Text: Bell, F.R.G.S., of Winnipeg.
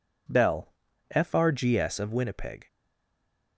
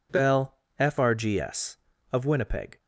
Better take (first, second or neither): second